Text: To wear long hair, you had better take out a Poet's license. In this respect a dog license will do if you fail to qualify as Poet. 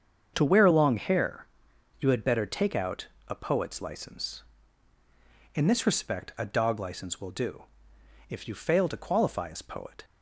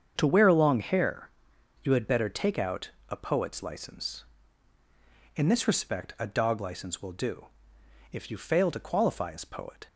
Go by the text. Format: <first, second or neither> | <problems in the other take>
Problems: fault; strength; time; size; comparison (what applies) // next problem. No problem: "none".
neither | starts louder than the rest; the same in both // pauses between "out" and "a"; slight; the same in both // pauses between "do" and "if"; noticeable; the same in both